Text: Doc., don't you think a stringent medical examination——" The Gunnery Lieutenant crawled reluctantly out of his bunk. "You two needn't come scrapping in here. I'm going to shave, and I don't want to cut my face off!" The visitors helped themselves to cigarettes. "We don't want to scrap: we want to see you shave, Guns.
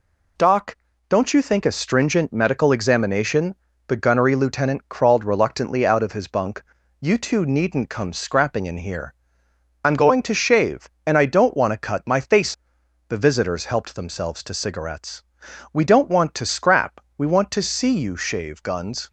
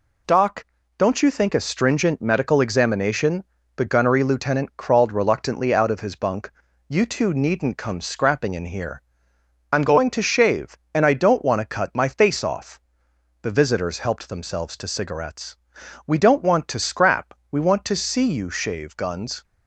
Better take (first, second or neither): second